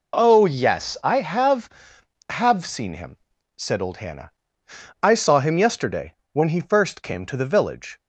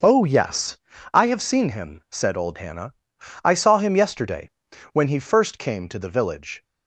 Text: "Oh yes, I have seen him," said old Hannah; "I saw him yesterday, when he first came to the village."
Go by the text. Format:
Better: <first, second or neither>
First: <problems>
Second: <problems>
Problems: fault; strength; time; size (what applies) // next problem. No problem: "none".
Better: second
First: says "have" twice; at 2.2 s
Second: none